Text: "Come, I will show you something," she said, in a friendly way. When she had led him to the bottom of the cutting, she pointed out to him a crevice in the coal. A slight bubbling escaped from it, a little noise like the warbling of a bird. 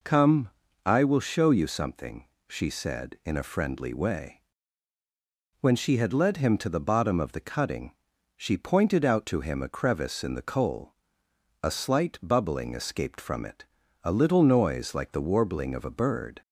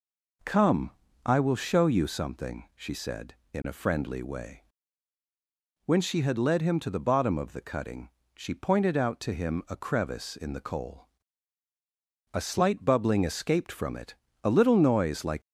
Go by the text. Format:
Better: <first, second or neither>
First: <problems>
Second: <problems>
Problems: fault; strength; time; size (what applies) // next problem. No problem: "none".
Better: first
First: none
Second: stops before "the warbling of a bird"; at 15.4 s